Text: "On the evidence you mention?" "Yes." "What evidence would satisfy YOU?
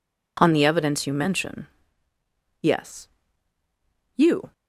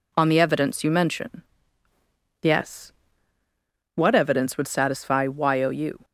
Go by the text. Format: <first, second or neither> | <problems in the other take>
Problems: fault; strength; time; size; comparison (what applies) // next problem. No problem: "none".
second | skips "What evidence would satisfy"; at 3.6 s